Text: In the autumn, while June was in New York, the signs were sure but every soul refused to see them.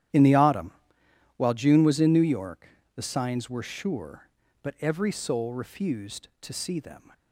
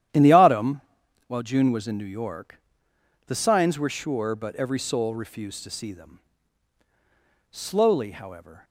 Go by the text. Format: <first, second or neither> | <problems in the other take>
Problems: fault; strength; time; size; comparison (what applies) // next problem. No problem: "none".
first | starts louder than the rest; strong; until 1.6 s; 11 dB; strong in the first // goes on to say "Slowly however"; noticeable; from 7.5 s on; 1.1 s long